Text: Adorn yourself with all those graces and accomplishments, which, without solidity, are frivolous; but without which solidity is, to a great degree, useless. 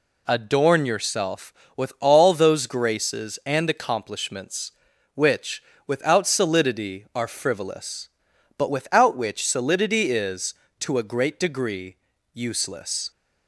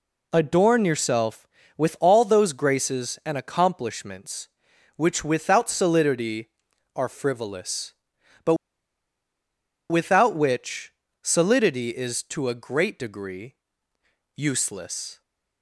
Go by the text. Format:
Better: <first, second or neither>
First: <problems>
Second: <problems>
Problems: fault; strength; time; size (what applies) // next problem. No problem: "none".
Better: first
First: none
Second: pauses between "but" and "without"; strong; at 8.5 s; 1.3 s long // pauses between "which" and "solidity"; slight; at 10.9 s; 0.30 s long